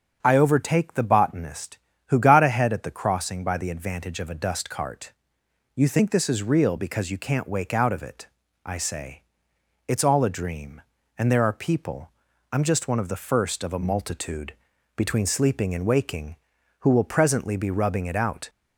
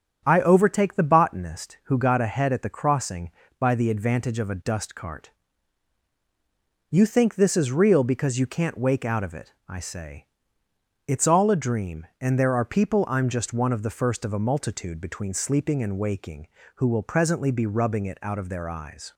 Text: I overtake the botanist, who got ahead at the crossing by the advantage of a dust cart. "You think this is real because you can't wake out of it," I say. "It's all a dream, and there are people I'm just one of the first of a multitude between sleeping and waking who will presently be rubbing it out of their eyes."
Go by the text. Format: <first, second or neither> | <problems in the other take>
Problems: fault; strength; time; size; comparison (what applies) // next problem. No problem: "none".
second | starts louder than the rest; strong; until 1.2 s; 7 dB; strong in the second // pauses between "people" and "I'm"; at 12.1 s; 0.40 s long // pauses between "multitude" and "between"; at 14.5 s; 0.42 s long // stops before "of their eyes"; at 18.4 s